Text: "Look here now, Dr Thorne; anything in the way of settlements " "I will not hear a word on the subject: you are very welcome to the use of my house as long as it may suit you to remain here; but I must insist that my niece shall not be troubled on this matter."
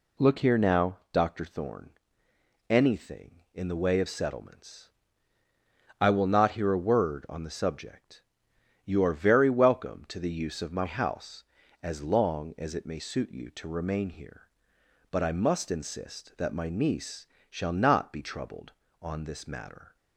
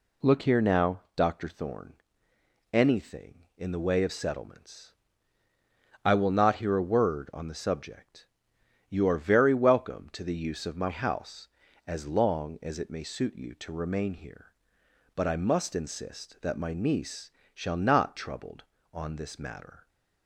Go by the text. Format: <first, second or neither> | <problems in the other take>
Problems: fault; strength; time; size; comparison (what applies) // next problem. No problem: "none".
first | pauses between "niece" and "shall"; slight; at 17.3 s; 0.24 s long; slight in the first // skips "be"; at 18.1 s